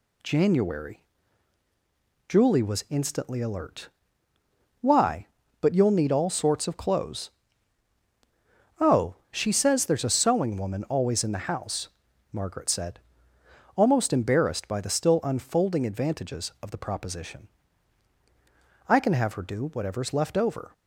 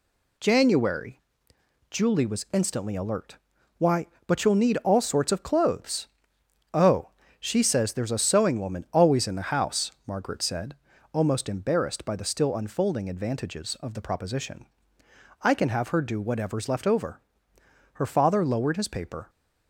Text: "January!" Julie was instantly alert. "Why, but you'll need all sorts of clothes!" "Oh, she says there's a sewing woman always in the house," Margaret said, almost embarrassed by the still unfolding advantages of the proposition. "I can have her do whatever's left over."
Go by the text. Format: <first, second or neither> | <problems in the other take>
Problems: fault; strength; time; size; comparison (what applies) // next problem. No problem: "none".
first | goes on to say "Her father lowered his paper"; from 17.9 s on; 1.3 s long